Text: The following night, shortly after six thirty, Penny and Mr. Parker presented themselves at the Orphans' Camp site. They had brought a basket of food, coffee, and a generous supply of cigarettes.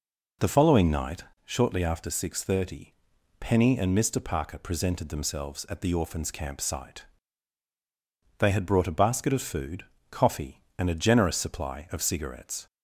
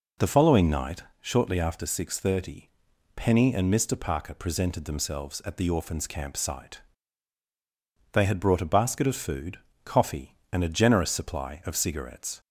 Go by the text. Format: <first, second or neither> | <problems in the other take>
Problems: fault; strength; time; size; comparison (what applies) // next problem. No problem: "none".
neither | none